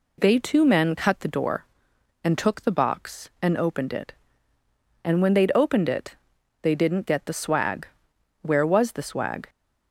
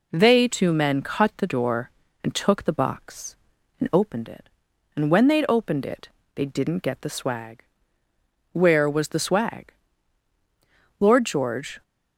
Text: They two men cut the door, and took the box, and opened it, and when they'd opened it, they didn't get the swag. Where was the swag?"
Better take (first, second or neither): first